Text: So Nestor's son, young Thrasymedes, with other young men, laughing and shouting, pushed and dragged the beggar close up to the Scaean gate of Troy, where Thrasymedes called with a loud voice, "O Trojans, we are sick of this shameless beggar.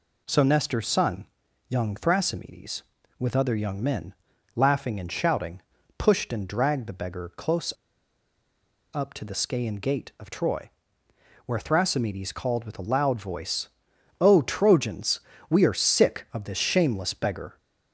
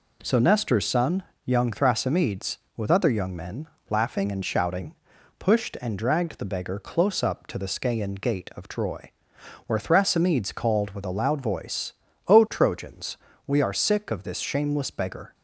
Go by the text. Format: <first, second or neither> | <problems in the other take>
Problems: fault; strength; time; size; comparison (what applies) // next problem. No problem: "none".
second | pauses between "close" and "up"; at 7.7 s; 1.2 s long